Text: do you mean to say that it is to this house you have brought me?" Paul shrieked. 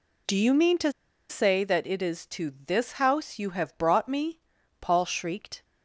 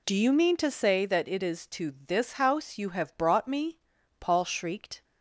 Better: second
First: pauses between "to" and "say"; at 0.9 s; 0.38 s long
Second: none

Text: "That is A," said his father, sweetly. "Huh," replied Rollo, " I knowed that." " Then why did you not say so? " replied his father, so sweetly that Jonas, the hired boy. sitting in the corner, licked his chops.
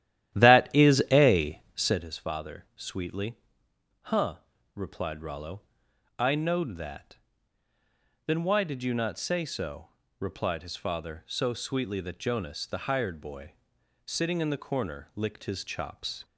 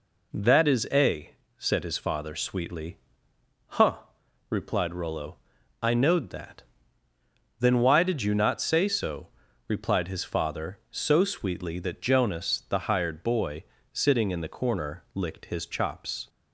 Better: second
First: starts louder than the rest; strong; until 2.1 s; 13 dB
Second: none

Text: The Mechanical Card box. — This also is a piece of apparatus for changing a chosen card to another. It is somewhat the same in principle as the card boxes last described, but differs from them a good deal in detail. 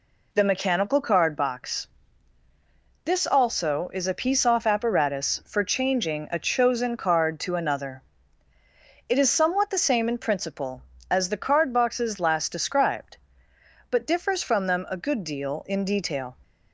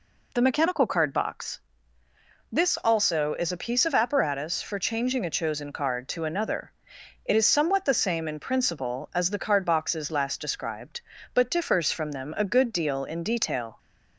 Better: second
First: says "off" for "of"; at 4.4 s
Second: none

